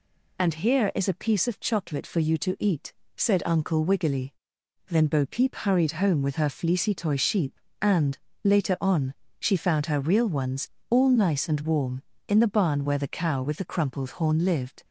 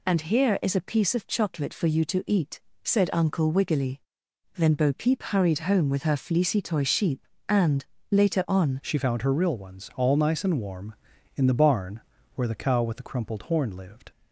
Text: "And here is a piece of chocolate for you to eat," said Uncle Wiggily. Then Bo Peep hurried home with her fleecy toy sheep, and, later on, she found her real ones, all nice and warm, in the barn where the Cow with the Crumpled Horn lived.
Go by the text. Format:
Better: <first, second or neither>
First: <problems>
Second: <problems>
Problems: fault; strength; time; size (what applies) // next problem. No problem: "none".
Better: first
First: none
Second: changes voice at "she"; from 8.8 s on; 5.3 s long // pauses between "barn" and "where"; slight; at 12.0 s; 0.34 s long